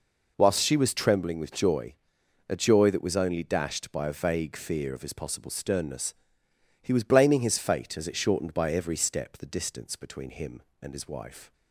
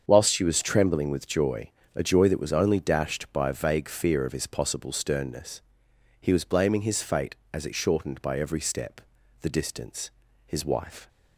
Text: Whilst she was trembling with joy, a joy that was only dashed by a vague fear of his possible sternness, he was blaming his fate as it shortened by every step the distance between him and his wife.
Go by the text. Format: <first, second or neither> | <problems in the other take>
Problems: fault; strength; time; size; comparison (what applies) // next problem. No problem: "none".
first | starts louder than the rest; strong; until 1.0 s; 7 dB // pauses between "step" and "the"; at 8.9 s; 0.42 s long // skips "between him and"; at 10.2 s